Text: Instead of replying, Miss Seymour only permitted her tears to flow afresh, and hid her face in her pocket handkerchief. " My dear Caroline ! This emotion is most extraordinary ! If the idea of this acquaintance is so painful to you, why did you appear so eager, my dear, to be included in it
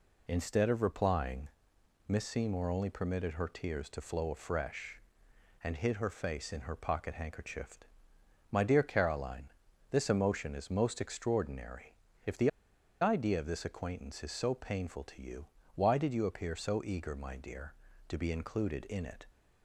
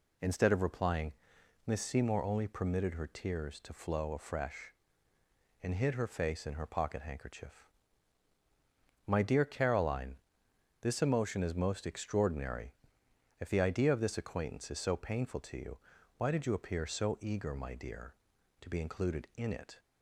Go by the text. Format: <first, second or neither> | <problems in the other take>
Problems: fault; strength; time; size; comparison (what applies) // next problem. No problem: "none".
second | pauses between "the" and "idea"; noticeable; at 12.4 s; 0.51 s long